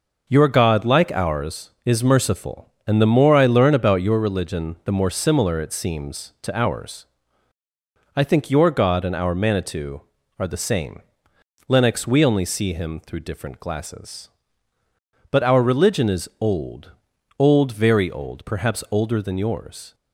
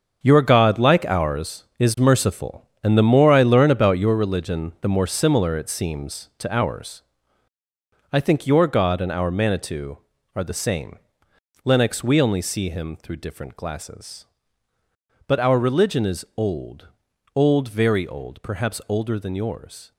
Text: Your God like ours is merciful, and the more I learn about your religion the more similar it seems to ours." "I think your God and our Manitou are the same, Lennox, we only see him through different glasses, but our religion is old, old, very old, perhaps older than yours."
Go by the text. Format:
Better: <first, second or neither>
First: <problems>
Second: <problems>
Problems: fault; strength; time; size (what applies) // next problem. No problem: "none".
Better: first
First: none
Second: gets quieter; strong; throughout; 10.5 dB